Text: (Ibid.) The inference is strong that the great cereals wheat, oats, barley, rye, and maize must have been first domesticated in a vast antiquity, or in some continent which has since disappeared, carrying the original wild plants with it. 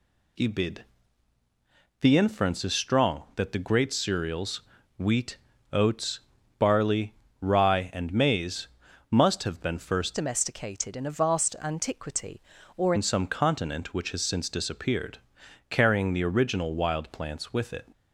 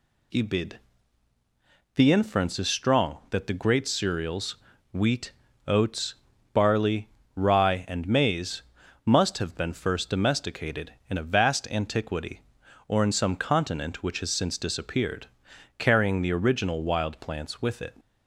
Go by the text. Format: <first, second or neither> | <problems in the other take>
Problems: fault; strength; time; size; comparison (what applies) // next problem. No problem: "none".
second | pauses between "cereals" and "wheat"; at 4.6 s; 0.38 s long; also in the second // pauses between "maize" and "must"; at 8.6 s; 0.42 s long; also in the second // changes voice from "domesticated" to "or"; from 10.1 to 12.9 s; 2.8 s long